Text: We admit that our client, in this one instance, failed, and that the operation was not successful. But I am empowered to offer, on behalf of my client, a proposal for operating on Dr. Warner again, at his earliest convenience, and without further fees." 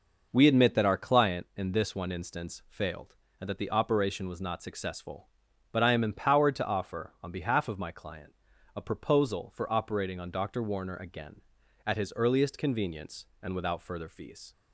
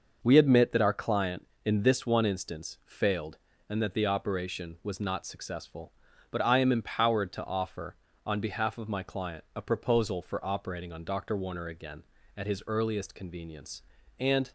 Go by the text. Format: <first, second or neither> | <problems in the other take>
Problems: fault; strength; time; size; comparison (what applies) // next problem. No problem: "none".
first | starts louder than the rest; noticeable; until 1.2 s; 6 dB // stops before "without further fees"; at 14.4 s